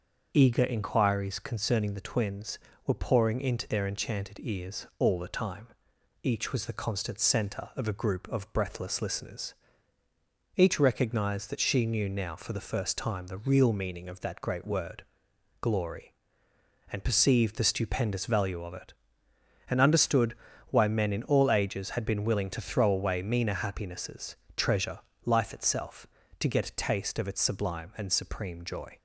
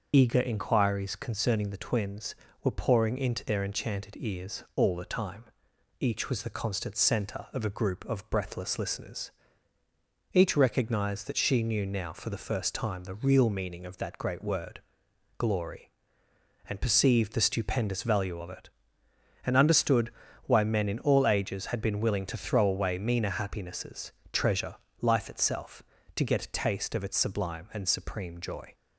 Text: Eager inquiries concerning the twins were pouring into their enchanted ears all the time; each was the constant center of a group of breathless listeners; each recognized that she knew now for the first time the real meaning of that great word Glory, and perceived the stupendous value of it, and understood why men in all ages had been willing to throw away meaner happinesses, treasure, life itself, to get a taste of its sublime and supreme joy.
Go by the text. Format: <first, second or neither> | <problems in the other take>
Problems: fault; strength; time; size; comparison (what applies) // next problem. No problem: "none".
first | loses the start of "Eager"; at 0.1 s; 25 ms // starts louder than the rest; noticeable; until 1.1 s; 6 dB; noticeable in the first // pauses between "word" and "Glory"; noticeable; at 14.7 s; 0.60 s long; noticeable in the first // pauses between "understood" and "why"; slight; at 20.1 s; 0.34 s long; slight in the first